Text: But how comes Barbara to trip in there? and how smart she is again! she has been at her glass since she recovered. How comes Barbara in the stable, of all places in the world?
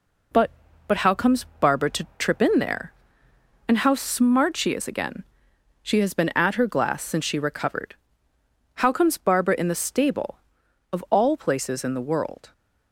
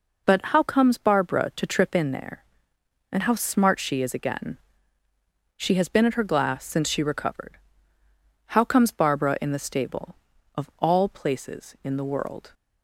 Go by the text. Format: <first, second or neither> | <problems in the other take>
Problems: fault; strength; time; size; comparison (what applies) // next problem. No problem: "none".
second | says "But" twice; at 0.8 s // pauses between "comes" and "Barbara"; slight; at 1.4 s; 0.16 s long